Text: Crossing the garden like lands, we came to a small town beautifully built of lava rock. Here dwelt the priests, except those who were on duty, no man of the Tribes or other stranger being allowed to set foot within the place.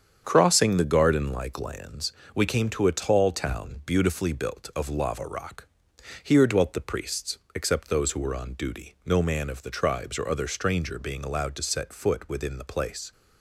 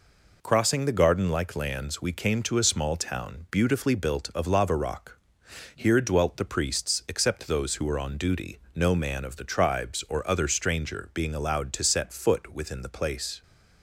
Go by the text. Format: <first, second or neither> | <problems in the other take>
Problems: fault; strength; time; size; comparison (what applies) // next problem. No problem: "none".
second | starts louder than the rest; strong; until 1.2 s; 8 dB // says "tall" for "small"; at 2.9 s